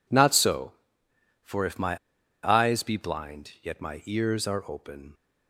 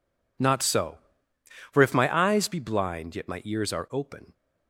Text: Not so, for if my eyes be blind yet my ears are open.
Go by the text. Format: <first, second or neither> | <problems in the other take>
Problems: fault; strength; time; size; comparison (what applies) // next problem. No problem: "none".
second | pauses between "my" and "eyes"; noticeable; at 1.9 s; 0.47 s long